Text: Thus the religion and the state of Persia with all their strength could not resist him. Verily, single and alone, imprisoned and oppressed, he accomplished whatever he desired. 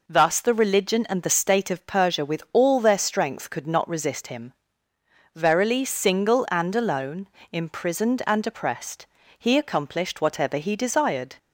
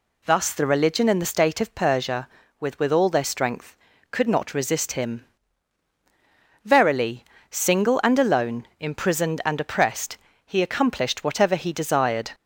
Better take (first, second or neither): first